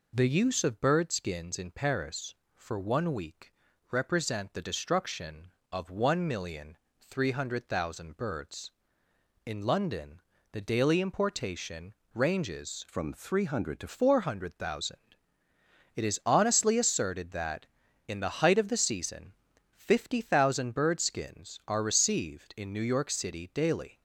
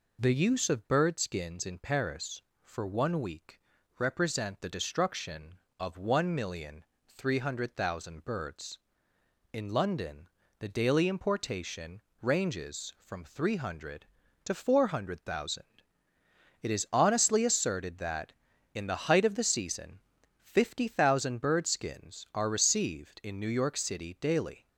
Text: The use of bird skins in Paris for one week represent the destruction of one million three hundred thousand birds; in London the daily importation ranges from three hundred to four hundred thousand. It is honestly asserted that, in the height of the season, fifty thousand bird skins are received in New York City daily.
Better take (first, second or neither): second